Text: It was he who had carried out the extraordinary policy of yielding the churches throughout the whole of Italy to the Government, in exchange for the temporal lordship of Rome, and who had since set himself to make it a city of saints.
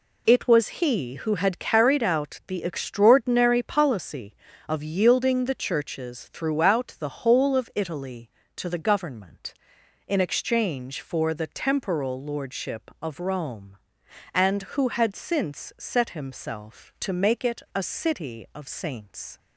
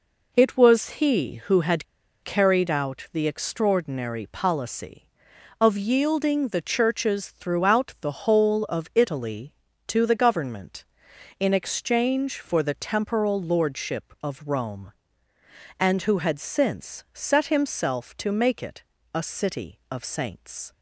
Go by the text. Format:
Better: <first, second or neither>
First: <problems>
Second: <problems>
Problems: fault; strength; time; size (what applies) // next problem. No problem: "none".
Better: first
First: none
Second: pauses between "had" and "carried"; at 1.8 s; 0.38 s long // pauses between "it" and "a"; slight; at 18.8 s; 0.28 s long